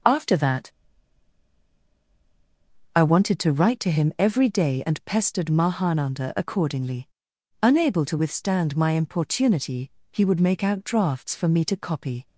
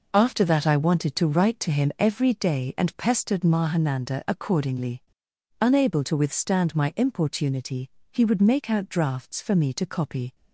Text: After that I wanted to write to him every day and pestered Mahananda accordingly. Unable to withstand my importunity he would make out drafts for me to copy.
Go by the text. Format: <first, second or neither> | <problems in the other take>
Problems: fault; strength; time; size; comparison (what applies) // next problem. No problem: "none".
second | pauses between "that" and "I"; strong; at 0.7 s; 2.2 s long // pauses between "importunity" and "he"; slight; at 9.8 s; 0.20 s long; slight in the second